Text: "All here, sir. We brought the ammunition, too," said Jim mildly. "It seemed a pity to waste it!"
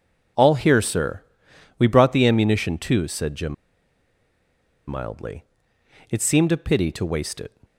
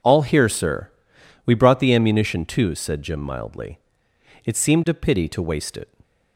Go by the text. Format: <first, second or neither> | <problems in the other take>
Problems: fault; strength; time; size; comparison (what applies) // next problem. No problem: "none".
second | pauses between "Jim" and "mildly"; strong; at 3.5 s; 1.3 s long